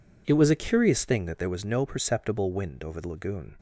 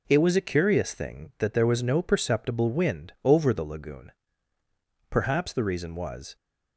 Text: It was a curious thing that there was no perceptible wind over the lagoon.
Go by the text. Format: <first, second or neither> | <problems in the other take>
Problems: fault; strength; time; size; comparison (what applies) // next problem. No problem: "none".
first | goes on to say "Perhaps the reason was"; noticeable; from 5.0 s on; 1.2 s long